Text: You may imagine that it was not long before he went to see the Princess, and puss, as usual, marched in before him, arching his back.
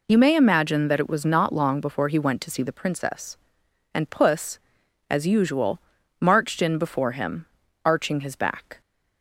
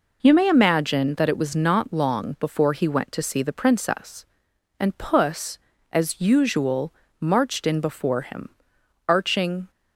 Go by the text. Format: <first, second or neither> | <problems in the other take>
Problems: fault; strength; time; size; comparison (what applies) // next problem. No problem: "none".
first | stops before "his back"; at 9.6 s